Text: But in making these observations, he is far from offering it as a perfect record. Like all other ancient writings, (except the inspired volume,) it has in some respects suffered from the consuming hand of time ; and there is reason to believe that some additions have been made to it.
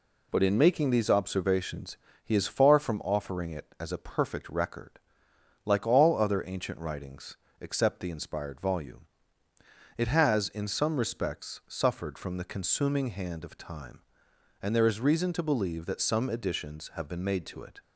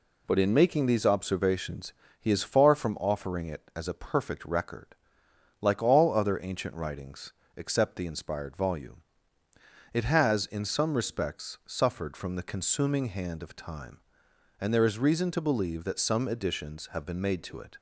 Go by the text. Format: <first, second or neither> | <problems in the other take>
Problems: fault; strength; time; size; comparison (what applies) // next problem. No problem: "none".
neither | none